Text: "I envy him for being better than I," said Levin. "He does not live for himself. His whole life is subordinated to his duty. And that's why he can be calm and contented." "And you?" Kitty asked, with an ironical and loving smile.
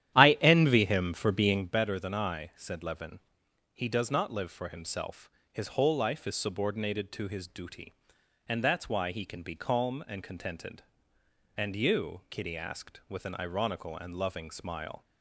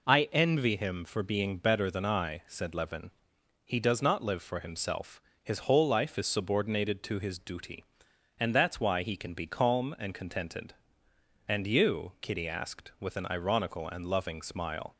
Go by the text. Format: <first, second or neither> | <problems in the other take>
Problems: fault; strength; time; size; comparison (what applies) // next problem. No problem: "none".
second | starts louder than the rest; strong; until 1.7 s; 11.5 dB